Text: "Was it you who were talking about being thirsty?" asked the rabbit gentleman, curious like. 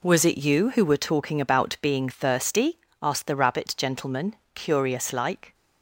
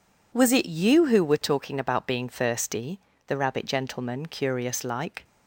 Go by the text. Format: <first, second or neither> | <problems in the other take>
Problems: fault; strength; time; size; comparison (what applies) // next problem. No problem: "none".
first | skips "asked"; at 3.1 s